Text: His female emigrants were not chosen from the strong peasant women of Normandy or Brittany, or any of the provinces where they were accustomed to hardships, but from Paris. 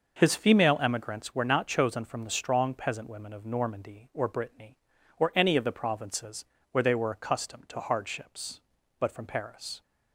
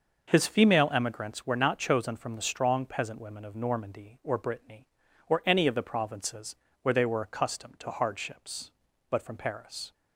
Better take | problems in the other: neither | pauses between "provinces" and "where"; slight; the same in both

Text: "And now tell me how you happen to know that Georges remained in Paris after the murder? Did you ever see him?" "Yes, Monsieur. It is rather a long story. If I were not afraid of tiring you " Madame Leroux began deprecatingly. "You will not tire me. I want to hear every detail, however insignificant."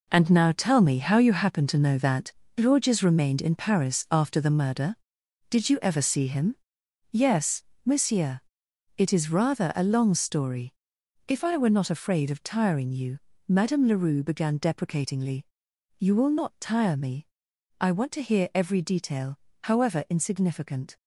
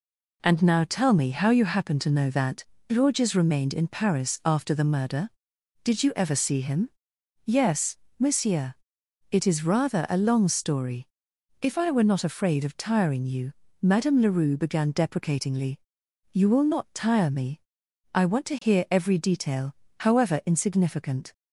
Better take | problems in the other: second | gets quieter; strong; throughout; 9.5 dB // pauses between "that" and "Georges"; slight; at 2.3 s; 0.26 s long; slight in the second

